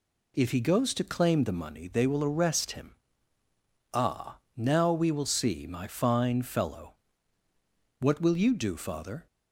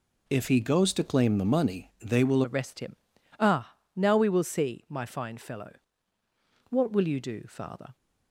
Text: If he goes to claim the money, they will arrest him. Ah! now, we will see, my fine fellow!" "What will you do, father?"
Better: first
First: none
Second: changes voice at "arrest"; from 2.4 s on; 5.5 s long

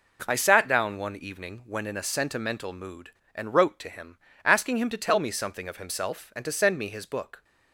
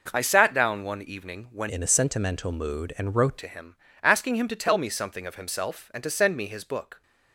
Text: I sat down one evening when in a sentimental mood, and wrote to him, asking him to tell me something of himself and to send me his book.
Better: first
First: none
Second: changes voice from "in" to "wrote"; from 1.6 to 3.3 s; 1.7 s long

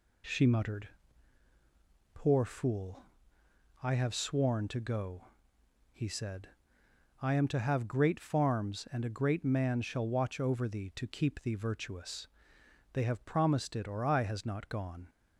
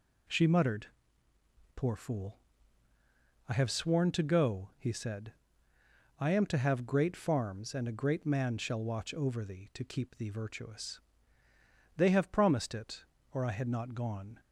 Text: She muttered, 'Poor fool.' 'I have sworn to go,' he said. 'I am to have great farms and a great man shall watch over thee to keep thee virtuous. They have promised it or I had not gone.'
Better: second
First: says "has" for "had"; at 14.2 s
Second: none

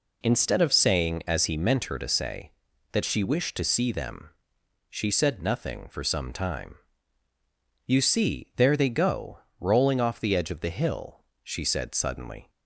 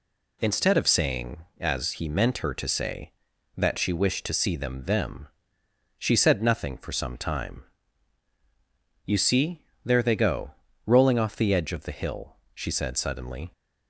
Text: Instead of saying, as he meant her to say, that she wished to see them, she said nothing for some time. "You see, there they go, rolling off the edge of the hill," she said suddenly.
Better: first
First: none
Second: says "them" twice; at 4.8 s

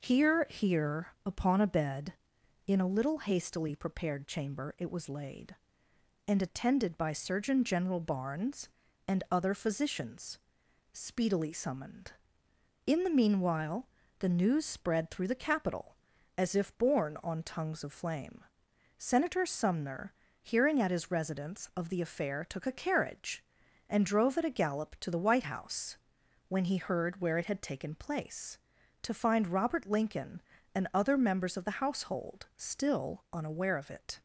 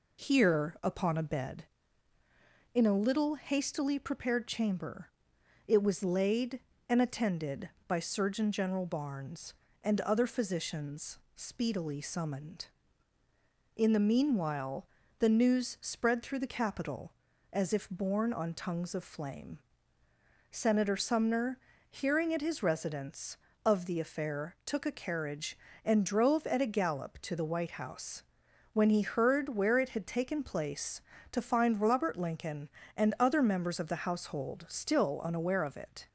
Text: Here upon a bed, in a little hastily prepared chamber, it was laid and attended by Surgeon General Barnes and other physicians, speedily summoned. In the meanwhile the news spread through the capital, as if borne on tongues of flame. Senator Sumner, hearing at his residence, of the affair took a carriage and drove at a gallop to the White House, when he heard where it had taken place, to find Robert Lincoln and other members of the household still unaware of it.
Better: second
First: says "Here" twice; at 0.4 s // pauses between "meanwhile" and "the"; slight; at 13.8 s; 0.32 s long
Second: pauses between "meanwhile" and "the"; slight; at 14.8 s; 0.30 s long

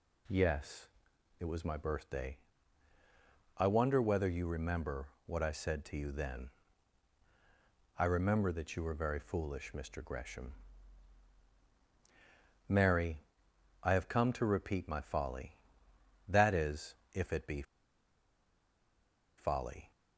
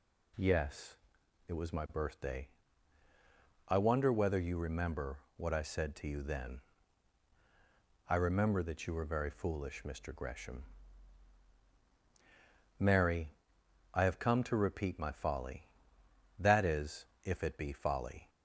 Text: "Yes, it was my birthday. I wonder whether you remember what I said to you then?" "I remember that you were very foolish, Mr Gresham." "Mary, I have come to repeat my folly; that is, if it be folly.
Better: second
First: pauses between "remember" and "what"; slight; at 5.0 s; 0.20 s long // pauses between "be" and "folly"; strong; at 17.6 s; 1.7 s long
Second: pauses between "remember" and "what"; slight; at 5.1 s; 0.20 s long

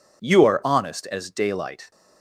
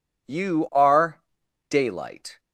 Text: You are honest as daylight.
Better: first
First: none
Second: skips "honest as"; at 1.4 s

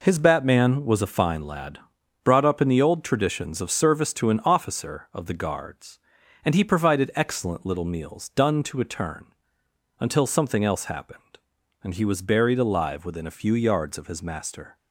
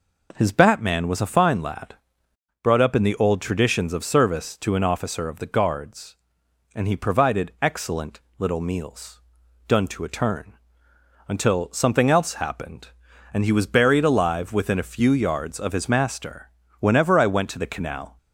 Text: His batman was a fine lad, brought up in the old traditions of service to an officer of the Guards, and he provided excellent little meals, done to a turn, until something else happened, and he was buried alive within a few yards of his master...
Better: first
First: none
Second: pauses between "excellent" and "little"; slight; at 8.1 s; 0.20 s long // goes on to say "Whenever I went to the canal"; from 16.7 s on; 1.3 s long

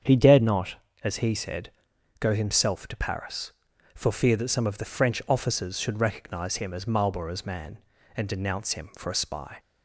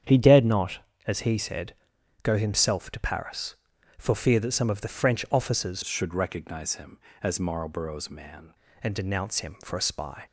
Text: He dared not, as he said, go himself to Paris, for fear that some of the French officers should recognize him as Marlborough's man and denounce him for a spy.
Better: first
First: starts louder than the rest; strong; until 1.3 s; 7.5 dB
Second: starts louder than the rest; strong; until 1.3 s; 8 dB // changes voice from "should" to "man"; from 5.8 to 8.5 s; 2.7 s long

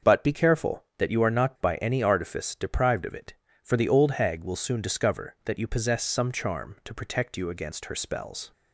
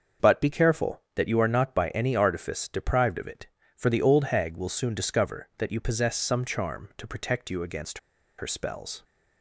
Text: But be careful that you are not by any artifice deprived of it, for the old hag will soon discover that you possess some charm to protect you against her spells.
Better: first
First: starts louder than the rest; until 1.1 s; 6.5 dB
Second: starts louder than the rest; until 1.3 s; 6.5 dB // pauses between "against" and "her"; at 7.9 s; 0.39 s long

